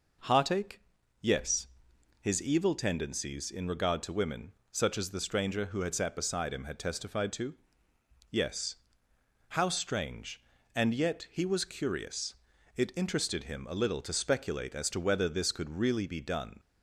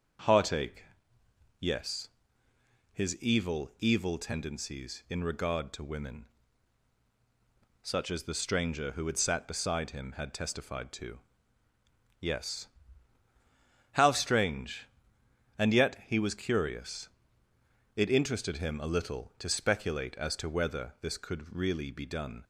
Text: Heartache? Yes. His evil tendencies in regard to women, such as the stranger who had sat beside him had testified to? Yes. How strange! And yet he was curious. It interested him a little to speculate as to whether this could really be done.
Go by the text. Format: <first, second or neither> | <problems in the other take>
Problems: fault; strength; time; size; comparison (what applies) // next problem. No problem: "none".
first | starts louder than the rest; until 2.0 s; 6.5 dB // says "evil" twice; at 3.8 s